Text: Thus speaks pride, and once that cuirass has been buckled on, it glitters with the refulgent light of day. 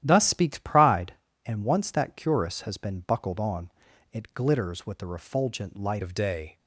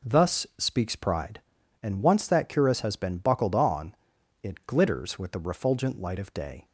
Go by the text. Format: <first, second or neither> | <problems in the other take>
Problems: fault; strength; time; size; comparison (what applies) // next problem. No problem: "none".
second | starts louder than the rest; strong; until 1.0 s; 11.5 dB // changes voice at "of"; from 6.0 s on; 0.5 s long